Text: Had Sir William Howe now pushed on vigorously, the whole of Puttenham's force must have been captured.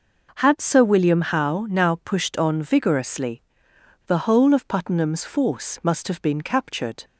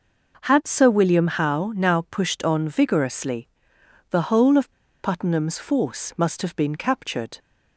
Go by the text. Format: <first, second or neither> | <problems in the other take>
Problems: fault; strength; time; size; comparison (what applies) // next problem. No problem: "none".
first | pauses between "of" and "Puttenham's"; slight; at 4.6 s; 0.33 s long